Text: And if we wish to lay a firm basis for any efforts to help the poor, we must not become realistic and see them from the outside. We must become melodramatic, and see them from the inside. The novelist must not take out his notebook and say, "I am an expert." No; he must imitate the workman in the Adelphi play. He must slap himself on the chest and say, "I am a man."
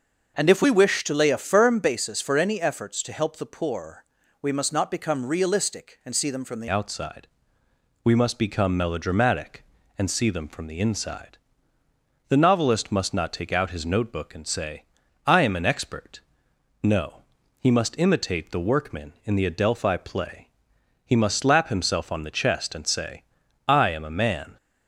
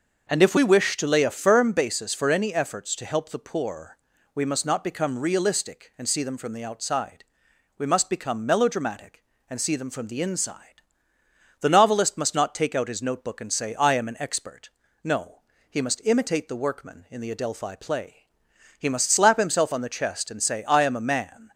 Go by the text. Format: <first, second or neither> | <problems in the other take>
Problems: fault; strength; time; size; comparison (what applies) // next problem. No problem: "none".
second | starts louder than the rest; noticeable; until 1.3 s; 6 dB; noticeable in the second // changes voice at "outside"; from 6.6 s on; 17.9 s long